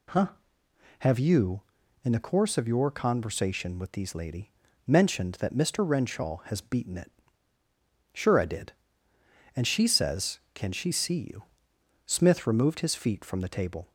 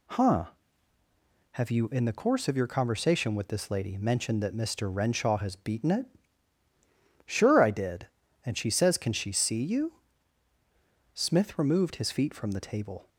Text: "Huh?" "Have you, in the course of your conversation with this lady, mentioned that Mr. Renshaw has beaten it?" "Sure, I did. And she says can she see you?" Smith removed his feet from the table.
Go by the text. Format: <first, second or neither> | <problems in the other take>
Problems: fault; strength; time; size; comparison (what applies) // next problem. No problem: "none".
second | says "these" for "this"; at 3.9 s